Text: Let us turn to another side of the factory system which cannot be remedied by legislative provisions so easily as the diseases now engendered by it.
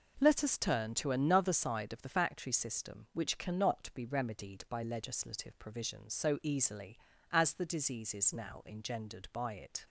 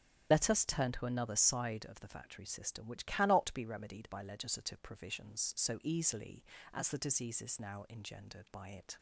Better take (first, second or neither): first